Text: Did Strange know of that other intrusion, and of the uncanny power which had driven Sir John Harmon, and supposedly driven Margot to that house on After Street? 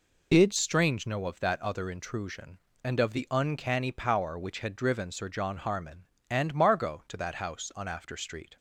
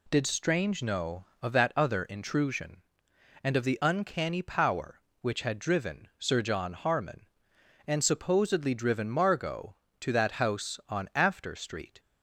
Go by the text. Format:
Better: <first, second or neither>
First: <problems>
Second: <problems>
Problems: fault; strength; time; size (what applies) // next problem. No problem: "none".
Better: second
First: skips "supposedly driven"; at 6.5 s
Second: none